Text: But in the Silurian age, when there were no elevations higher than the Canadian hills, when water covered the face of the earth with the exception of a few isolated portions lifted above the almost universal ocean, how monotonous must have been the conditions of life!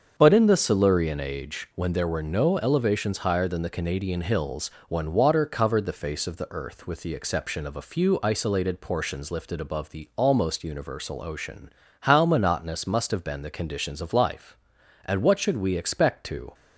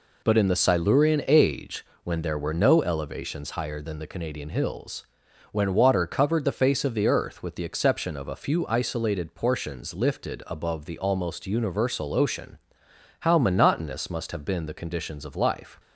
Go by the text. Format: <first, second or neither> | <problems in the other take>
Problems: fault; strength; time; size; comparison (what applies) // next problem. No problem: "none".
second | starts louder than the rest; until 1.1 s; 6.5 dB // goes on to say "And what should we expect to"; from 15.0 s on; 1.4 s long